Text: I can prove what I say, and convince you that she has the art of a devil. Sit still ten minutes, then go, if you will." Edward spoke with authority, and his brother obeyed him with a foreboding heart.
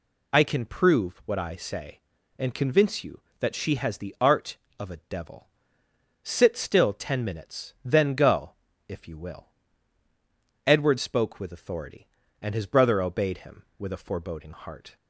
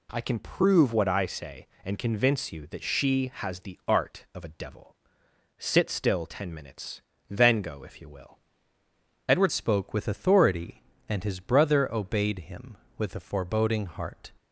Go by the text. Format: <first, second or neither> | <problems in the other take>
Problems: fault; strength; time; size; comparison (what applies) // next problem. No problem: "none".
first | changes voice at "spoke"; from 9.5 s on; 4.8 s long